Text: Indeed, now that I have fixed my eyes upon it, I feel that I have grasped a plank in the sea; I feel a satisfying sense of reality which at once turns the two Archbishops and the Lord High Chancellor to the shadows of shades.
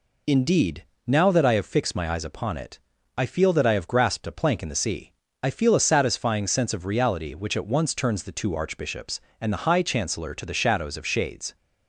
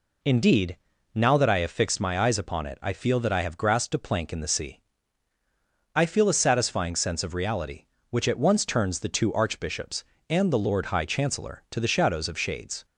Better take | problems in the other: second | skips "Lord"; at 9.6 s

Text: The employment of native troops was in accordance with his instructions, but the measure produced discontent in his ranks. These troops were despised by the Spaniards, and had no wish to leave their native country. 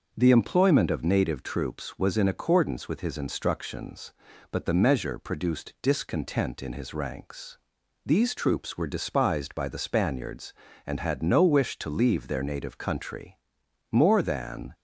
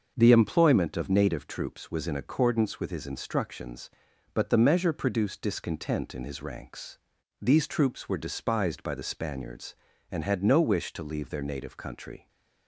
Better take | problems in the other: second | starts louder than the rest; noticeable; until 1.1 s; 6 dB; also in the second // goes on to say "More than"; noticeable; from 13.9 s on; 0.84 s long

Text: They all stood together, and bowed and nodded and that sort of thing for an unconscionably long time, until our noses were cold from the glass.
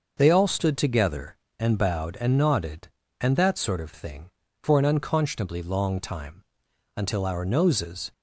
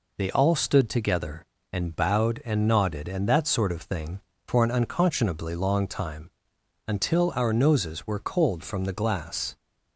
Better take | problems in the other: second | starts louder than the rest; noticeable; until 1.1 s; 6 dB // stops before "were cold from the glass"; at 8.1 s

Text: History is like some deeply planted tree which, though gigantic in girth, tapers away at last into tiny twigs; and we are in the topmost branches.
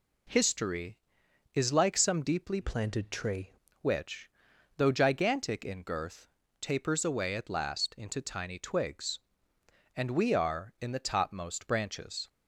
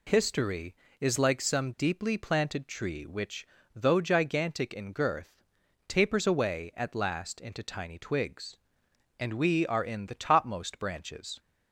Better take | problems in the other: second | changes voice from "planted" to "tree"; from 2.6 to 3.5 s; 0.9 s long

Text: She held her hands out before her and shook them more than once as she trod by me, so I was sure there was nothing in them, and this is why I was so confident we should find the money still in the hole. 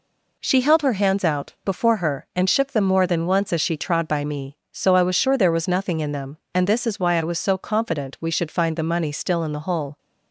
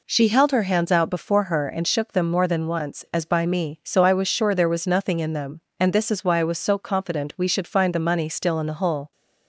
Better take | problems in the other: first | skips "she trod"; at 3.2 s

